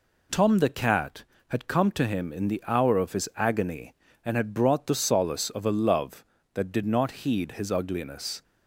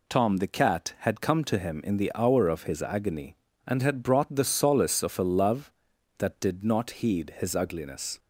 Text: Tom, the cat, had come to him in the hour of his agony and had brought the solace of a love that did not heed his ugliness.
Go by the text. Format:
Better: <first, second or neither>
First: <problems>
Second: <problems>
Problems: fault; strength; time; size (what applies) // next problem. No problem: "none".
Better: neither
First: none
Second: none